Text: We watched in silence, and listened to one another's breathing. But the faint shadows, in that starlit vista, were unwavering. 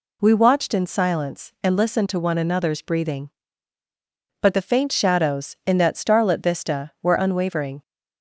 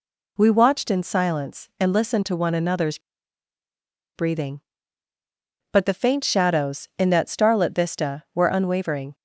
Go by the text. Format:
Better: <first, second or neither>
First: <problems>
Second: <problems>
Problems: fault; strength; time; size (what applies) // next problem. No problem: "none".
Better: first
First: none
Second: pauses between "another's" and "breathing"; at 2.9 s; 1.1 s long